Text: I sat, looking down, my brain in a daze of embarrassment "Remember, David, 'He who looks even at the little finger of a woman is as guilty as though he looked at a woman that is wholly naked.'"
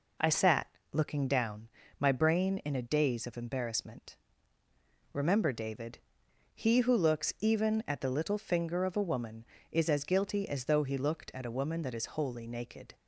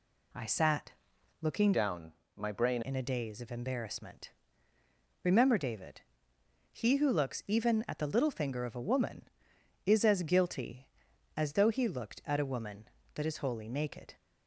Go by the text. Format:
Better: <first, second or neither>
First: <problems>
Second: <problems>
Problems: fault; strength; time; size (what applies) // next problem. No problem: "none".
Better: first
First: pauses between "embarrassment" and "Remember"; noticeable; at 4.1 s; 0.96 s long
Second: changes voice from "down" to "brain"; from 1.7 to 2.8 s; 1.1 s long // pauses between "embarrassment" and "Remember"; noticeable; at 4.3 s; 0.92 s long